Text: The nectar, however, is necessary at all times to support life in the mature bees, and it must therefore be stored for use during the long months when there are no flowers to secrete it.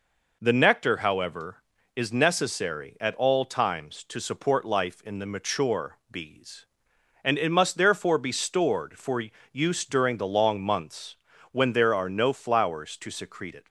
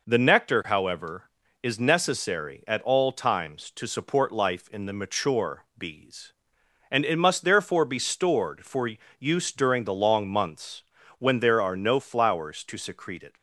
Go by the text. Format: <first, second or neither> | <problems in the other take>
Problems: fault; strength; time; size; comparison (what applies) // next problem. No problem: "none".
neither | pauses between "for" and "use"; slight; the same in both // pauses between "months" and "when"; the same in both